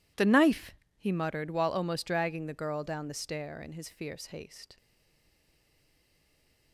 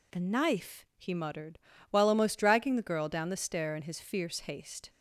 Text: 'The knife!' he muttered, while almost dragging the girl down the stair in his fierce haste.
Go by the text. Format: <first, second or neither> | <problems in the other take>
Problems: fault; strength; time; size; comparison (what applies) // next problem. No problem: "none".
second | stays silent after the last word; noticeable; from 4.7 s on; 2.0 s long